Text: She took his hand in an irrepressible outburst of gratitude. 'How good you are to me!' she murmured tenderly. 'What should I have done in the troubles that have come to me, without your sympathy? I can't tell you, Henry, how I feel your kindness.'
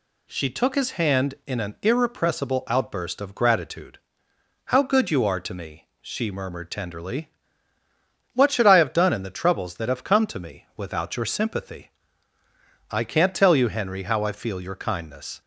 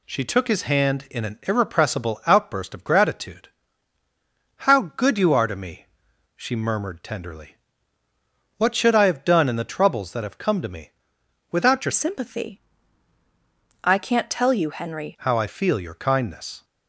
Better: first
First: none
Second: changes voice from "sympathy" to "Henry"; from 11.9 to 15.1 s; 3.2 s long

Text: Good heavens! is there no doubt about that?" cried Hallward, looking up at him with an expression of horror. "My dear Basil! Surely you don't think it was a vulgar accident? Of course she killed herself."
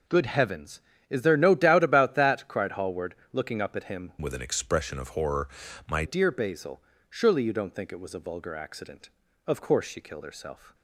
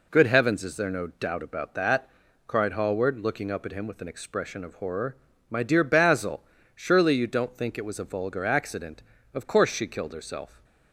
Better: second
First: changes voice from "with" to "My"; from 4.2 to 6.0 s; 1.8 s long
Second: none

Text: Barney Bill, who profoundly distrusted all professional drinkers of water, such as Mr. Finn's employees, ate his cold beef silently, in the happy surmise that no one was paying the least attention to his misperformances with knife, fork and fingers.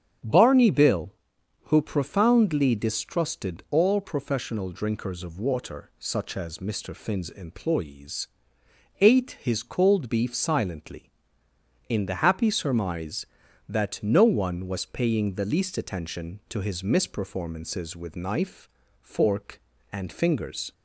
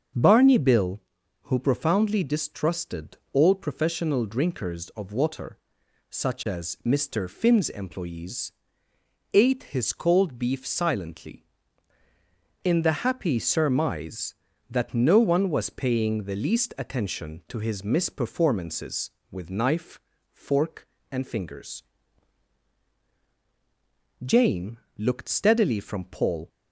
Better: first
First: starts louder than the rest; strong; until 1.7 s; 8.5 dB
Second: starts louder than the rest; until 1.5 s; 7 dB // pauses between "distrusted" and "all"; slight; at 3.1 s; 0.16 s long // goes on to say "Jane looked steadily from Paul"; strong; from 24.2 s on; 2.2 s long

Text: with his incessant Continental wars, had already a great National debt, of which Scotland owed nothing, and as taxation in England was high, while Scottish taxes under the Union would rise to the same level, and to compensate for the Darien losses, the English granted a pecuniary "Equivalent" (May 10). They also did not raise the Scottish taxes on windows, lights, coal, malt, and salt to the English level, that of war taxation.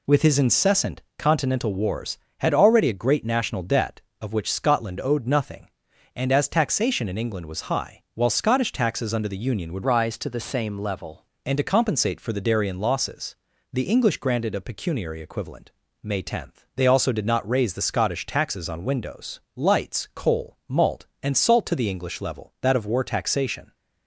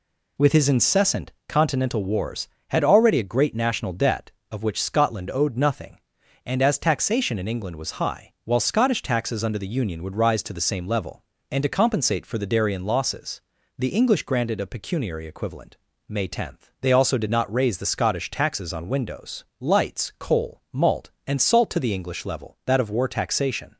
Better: second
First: pauses between "incessant" and "Continental"; slight; at 1.0 s; 0.16 s long // changes voice from "rise" to "level"; from 9.8 to 11.2 s; 1.4 s long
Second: pauses between "incessant" and "Continental"; slight; at 1.3 s; 0.16 s long

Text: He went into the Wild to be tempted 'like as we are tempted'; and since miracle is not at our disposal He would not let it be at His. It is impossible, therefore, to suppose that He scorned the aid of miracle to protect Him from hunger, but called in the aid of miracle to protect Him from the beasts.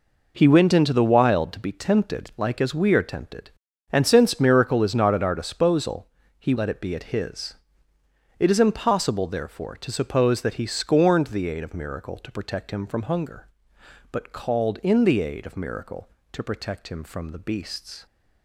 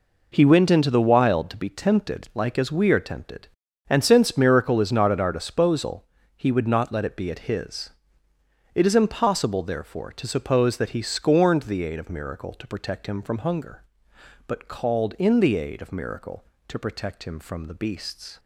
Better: second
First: pauses between "disposal" and "He"; slight; at 6.0 s; 0.30 s long // skips "would not"; at 6.5 s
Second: pauses between "disposal" and "He"; slight; at 6.0 s; 0.30 s long

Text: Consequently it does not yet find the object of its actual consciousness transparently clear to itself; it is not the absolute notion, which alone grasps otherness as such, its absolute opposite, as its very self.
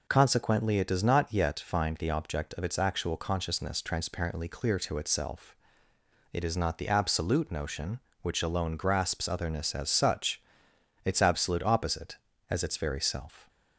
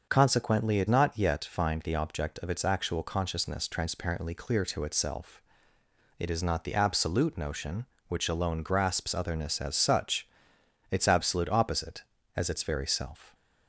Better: first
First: none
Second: starts louder than the rest; until 1.1 s; 6.5 dB // skips "does"; at 0.8 s

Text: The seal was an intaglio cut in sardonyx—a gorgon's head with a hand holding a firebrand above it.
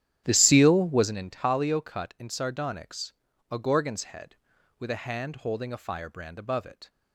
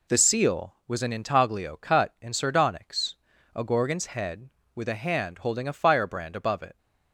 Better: second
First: starts louder than the rest; strong; until 1.1 s; 10.5 dB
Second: none

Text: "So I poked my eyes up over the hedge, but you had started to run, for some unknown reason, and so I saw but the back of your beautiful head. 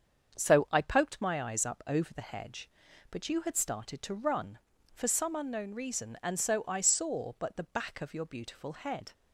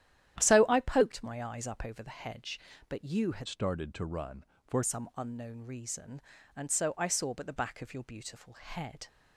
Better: first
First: starts louder than the rest; until 1.4 s; 7 dB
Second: starts louder than the rest; strong; until 1.4 s; 11.5 dB // changes voice from "started" to "for"; from 3.4 to 4.8 s; 1.4 s long

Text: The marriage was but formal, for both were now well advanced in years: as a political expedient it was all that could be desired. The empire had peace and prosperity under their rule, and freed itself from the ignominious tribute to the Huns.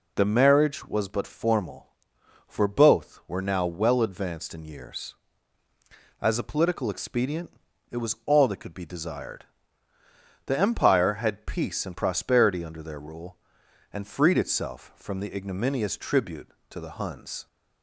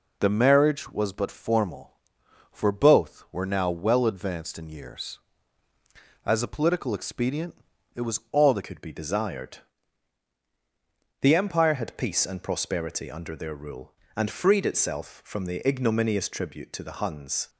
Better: first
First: pauses between "expedient" and "it"; at 7.5 s; 0.38 s long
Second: pauses between "expedient" and "it"; at 7.5 s; 0.38 s long // changes voice at "could"; from 8.6 s on; 8.8 s long

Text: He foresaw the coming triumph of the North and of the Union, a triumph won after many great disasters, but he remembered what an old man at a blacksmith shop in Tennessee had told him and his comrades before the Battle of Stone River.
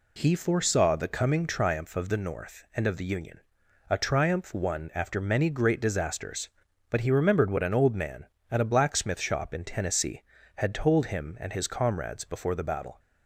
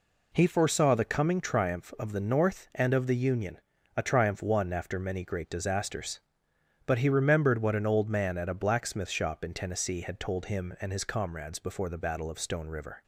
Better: second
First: stops before "of Stone River"; at 12.9 s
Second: none

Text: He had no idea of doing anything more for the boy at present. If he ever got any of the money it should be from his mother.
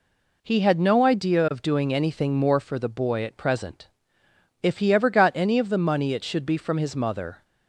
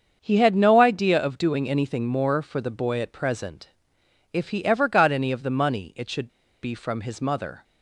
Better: first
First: none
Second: starts louder than the rest; until 1.2 s; 7 dB // pauses between "should" and "be"; slight; at 6.2 s; 0.35 s long

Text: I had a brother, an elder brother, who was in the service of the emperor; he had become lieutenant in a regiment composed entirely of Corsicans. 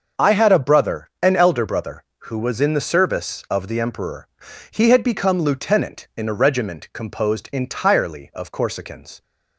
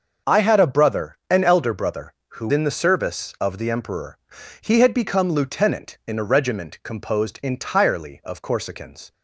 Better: first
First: starts louder than the rest; until 1.2 s; 6.5 dB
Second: starts louder than the rest; until 1.3 s; 6.5 dB // skips "was"; at 2.4 s

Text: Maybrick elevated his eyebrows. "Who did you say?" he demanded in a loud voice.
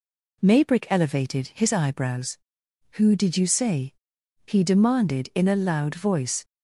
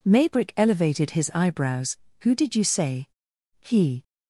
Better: first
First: none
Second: stops before "demanded in a loud voice"; at 4.0 s

